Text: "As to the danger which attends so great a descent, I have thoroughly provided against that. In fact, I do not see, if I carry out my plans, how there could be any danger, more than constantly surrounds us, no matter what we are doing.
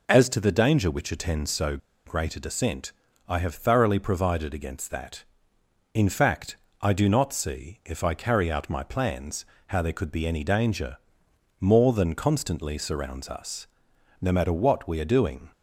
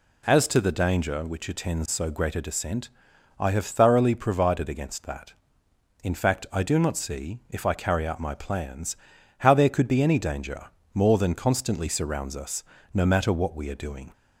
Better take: second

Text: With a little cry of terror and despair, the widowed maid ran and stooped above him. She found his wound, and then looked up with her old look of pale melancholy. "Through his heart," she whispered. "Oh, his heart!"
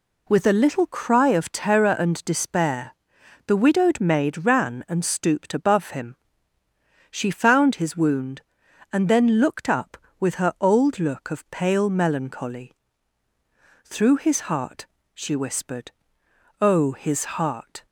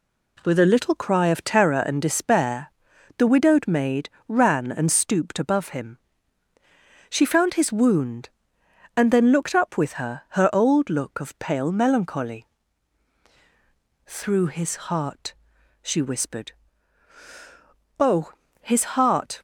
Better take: first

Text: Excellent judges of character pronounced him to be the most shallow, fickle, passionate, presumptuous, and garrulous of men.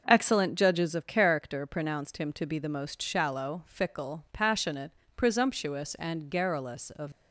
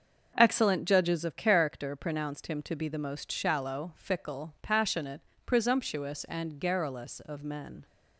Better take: second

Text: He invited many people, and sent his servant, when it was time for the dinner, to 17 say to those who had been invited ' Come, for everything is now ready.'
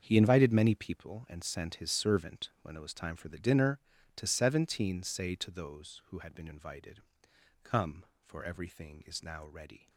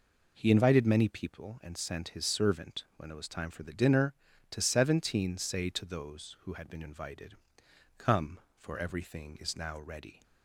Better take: second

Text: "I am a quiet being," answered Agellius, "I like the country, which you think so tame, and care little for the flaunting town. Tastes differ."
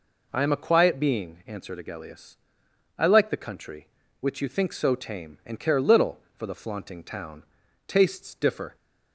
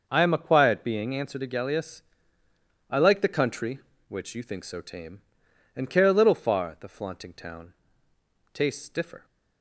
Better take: first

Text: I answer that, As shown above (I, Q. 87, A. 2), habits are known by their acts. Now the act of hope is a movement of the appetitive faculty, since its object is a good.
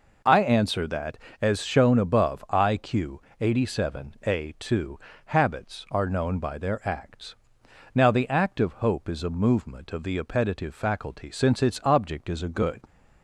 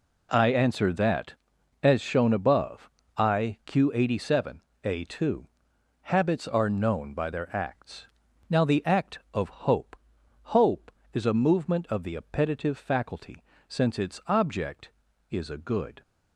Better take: first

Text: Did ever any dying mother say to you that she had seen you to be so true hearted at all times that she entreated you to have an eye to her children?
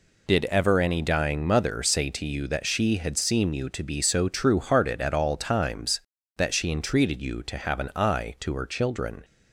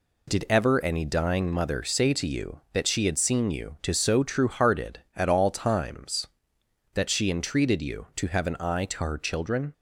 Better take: first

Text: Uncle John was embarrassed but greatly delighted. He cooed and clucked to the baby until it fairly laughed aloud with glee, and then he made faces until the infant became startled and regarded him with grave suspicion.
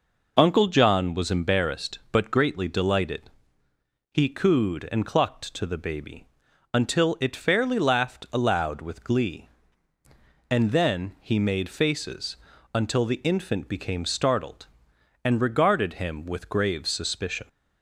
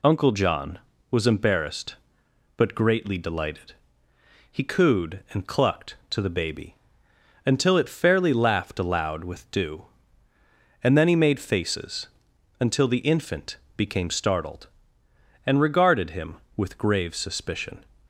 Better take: first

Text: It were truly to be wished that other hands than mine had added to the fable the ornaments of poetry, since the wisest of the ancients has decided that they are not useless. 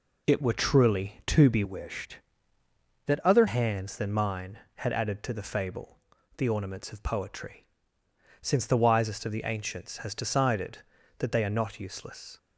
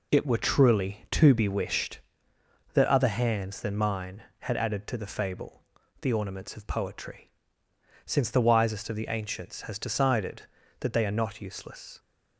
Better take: second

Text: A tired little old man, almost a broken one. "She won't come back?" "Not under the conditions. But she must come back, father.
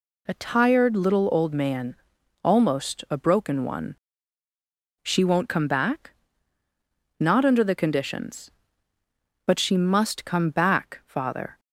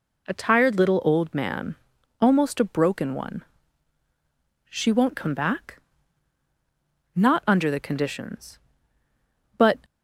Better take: first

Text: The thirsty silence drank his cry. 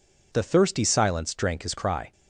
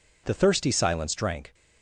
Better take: first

